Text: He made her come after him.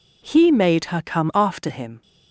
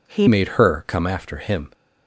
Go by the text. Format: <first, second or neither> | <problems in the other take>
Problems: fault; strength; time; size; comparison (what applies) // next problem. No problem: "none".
first | changes voice at "made"; from 0.2 s on; 1.4 s long